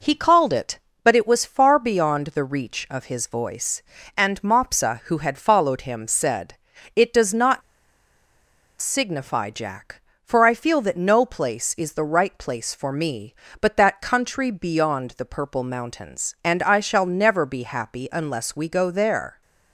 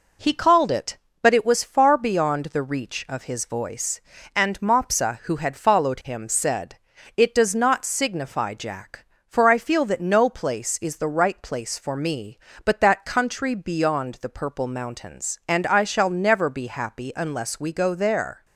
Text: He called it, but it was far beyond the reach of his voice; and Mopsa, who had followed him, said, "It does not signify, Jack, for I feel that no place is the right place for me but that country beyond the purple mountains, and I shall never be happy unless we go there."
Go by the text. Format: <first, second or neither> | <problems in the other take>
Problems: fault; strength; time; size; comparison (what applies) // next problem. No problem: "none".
second | pauses between "not" and "signify"; at 7.6 s; 1.1 s long